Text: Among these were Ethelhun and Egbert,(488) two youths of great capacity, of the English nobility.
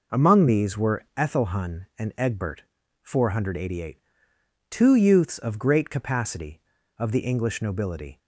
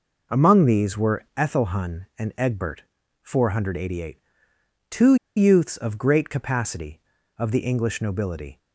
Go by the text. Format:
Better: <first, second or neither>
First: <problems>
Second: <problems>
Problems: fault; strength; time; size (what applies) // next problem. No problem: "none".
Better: first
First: none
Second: pauses between "two" and "youths"; slight; at 5.1 s; 0.21 s long